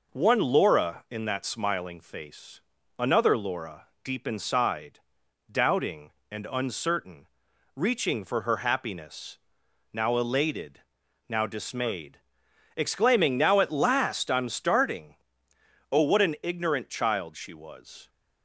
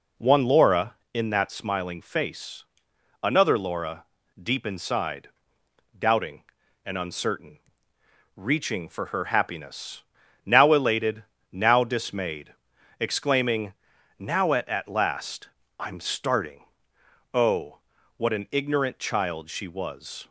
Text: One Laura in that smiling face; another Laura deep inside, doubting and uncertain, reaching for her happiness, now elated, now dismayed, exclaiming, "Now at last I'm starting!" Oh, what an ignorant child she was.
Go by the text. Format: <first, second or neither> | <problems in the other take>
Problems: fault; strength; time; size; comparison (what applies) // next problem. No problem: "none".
first | pauses between "Laura" and "deep"; at 4.0 s; 0.38 s long // says "at" twice; at 14.6 s // pauses between "last" and "I'm"; slight; at 15.4 s; 0.30 s long